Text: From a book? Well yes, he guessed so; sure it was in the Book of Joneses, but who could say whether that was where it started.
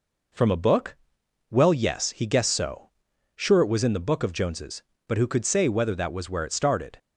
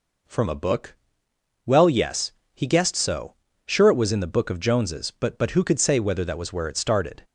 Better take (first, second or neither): first